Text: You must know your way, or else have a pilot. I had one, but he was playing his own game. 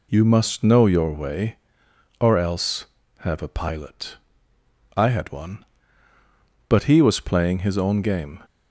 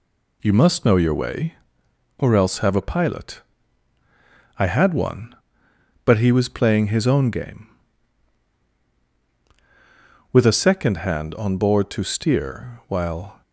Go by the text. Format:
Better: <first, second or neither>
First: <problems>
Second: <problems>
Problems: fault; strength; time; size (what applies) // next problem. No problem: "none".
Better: first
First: none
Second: goes on to say "With a second hand on board to steer while"; strong; from 10.3 s on; 3.1 s long